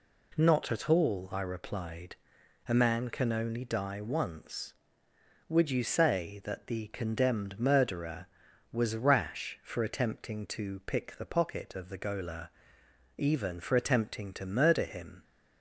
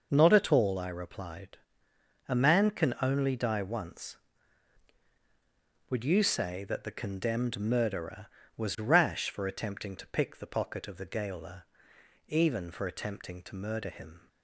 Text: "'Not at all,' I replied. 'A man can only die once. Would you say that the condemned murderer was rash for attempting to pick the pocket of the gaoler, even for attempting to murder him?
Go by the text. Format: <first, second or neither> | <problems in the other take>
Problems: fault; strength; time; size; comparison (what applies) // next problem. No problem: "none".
neither | none